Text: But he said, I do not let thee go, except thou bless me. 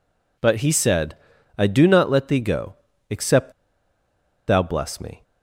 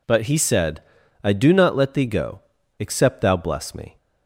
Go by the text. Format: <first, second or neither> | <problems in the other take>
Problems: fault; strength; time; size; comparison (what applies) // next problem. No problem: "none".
second | pauses between "except" and "thou"; noticeable; at 3.5 s; 0.96 s long